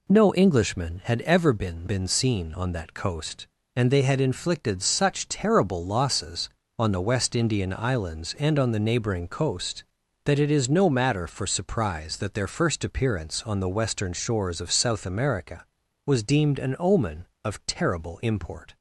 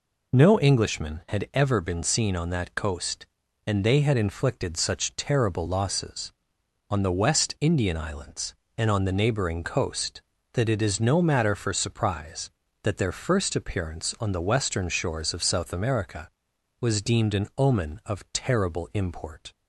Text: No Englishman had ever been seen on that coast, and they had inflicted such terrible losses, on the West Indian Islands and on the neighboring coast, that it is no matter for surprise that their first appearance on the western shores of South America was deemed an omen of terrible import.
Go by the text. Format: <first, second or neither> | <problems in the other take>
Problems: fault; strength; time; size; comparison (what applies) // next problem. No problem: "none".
second | says "been" twice; at 1.8 s